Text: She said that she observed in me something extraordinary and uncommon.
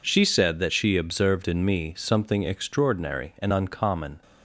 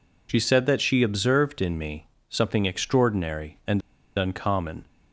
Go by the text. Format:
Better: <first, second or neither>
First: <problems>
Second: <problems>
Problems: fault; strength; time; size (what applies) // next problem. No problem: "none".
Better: first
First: none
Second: pauses between "me" and "something"; slight; at 2.0 s; 0.22 s long // pauses between "and" and "uncommon"; at 3.8 s; 0.36 s long